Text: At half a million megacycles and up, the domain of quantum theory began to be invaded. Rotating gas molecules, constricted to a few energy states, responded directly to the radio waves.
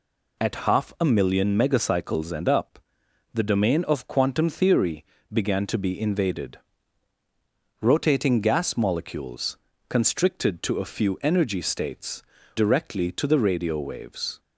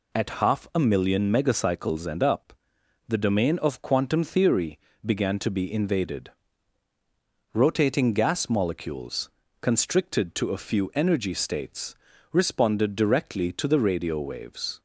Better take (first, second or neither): second